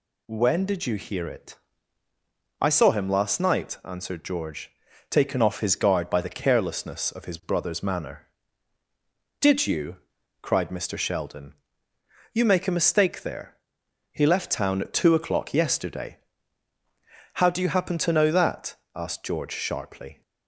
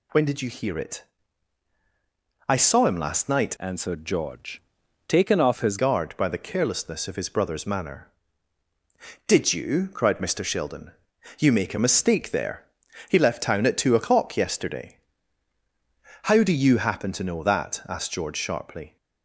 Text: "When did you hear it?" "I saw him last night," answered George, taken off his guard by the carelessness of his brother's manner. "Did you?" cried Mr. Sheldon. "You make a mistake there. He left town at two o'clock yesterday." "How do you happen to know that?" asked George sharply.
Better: first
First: none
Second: changes voice from "answered" to "his"; from 3.5 to 5.7 s; 2.2 s long

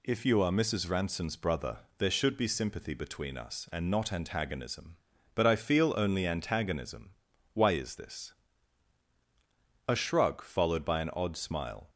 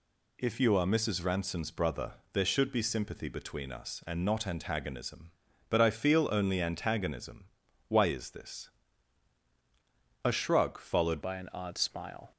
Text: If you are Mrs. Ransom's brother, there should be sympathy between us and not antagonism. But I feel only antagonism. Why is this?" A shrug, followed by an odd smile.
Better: first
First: none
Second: changes voice at "by"; from 11.2 s on; 1.1 s long

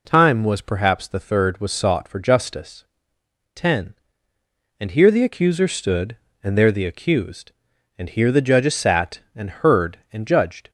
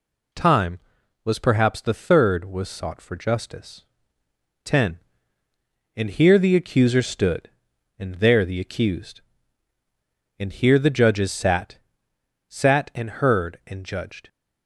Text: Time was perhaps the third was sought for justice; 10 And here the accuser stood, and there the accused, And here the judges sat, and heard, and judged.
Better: first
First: none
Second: says "sat" twice; at 12.4 s

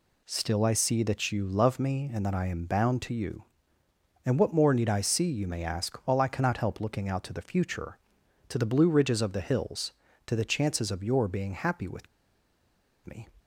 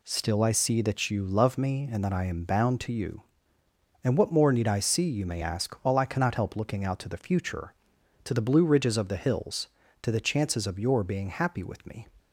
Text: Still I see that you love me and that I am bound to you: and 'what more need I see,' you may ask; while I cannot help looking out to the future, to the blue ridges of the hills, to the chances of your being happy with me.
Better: second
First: pauses between "with" and "me"; at 12.0 s; 0.98 s long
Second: none

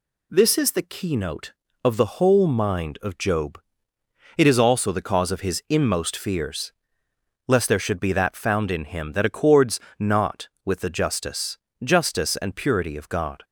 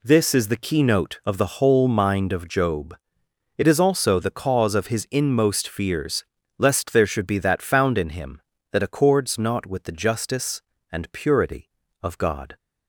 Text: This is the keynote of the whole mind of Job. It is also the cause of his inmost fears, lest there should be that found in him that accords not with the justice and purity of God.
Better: second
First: pauses between "accords" and "not"; slight; at 9.7 s; 0.18 s long // says "justice" twice; at 11.8 s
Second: none

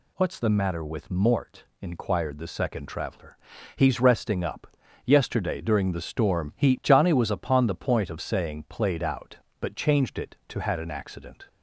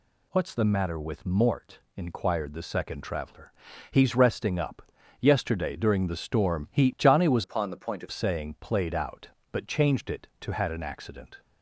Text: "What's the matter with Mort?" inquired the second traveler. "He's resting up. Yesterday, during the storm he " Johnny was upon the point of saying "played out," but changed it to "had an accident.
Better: first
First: none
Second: changes voice from "upon" to "of"; from 7.4 to 8.0 s; 0.6 s long

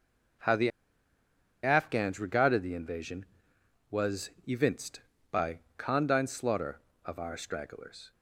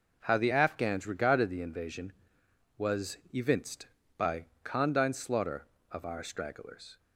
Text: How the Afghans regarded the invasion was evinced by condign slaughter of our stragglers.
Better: second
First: pauses between "the" and "Afghans"; noticeable; at 0.6 s; 0.94 s long // pauses between "was" and "evinced"; slight; at 4.2 s; 0.16 s long // pauses between "by" and "condign"; slight; at 5.5 s; 0.18 s long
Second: pauses between "was" and "evinced"; slight; at 3.1 s; 0.15 s long // pauses between "by" and "condign"; slight; at 4.4 s; 0.18 s long

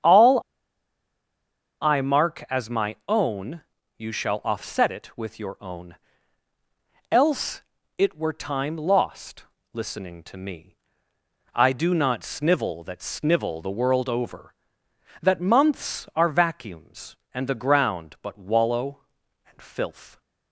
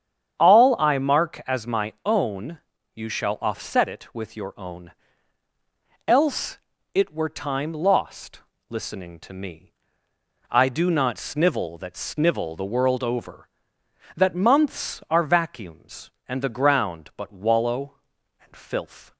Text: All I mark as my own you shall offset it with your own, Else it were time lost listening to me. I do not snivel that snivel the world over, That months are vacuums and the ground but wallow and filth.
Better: second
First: starts louder than the rest; strong; until 2.4 s; 8 dB // pauses between "All" and "I"; strong; at 0.3 s; 1.4 s long // pauses between "own" and "you"; slight; at 3.6 s; 0.34 s long // pauses between "Else" and "it"; slight; at 7.6 s; 0.34 s long // pauses between "lost" and "listening"; slight; at 9.4 s; 0.28 s long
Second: starts louder than the rest; strong; until 1.4 s; 8 dB // pauses between "own" and "you"; slight; at 2.5 s; 0.34 s long // pauses between "Else" and "it"; slight; at 6.5 s; 0.34 s long // pauses between "lost" and "listening"; slight; at 8.4 s; 0.28 s long

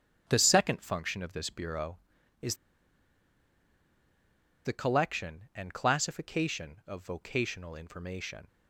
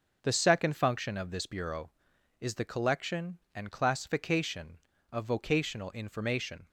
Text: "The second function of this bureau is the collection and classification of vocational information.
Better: second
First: starts louder than the rest; until 1.2 s; 7 dB // pauses between "is" and "the"; strong; at 2.5 s; 2.1 s long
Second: starts louder than the rest; noticeable; until 1.2 s; 6 dB

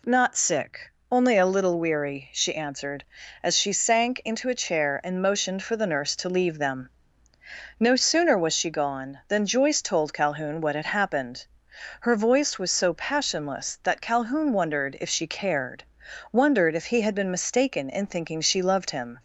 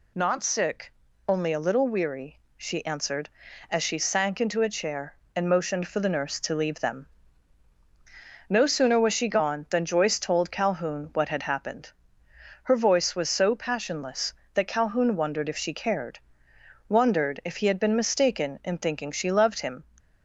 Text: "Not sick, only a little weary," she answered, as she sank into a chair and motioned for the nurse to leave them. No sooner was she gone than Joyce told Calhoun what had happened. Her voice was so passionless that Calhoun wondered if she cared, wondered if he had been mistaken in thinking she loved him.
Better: neither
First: none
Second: none

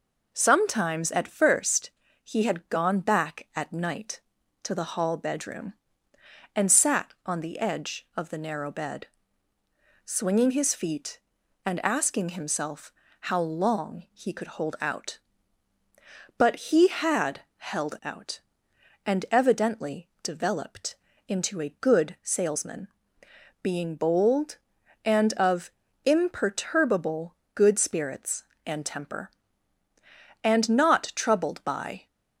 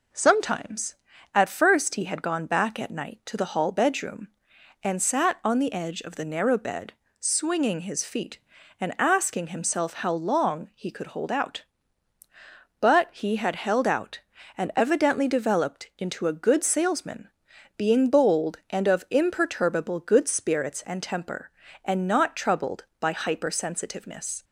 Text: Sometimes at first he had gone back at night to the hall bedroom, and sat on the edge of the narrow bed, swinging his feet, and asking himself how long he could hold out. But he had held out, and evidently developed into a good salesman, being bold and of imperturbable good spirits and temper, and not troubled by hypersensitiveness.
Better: second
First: pauses between "first" and "he"; slight; at 1.8 s; 0.34 s long // pauses between "himself" and "how"; slight; at 12.9 s; 0.30 s long // pauses between "had" and "held"; slight; at 17.4 s; 0.16 s long // pauses between "developed" and "into"; slight; at 20.9 s; 0.32 s long // pauses between "of" and "imperturbable"; slight; at 25.7 s; 0.34 s long // pauses between "imperturbable" and "good"; slight; at 27.3 s; 0.20 s long // stops before "hypersensitiveness"; at 32.0 s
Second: none

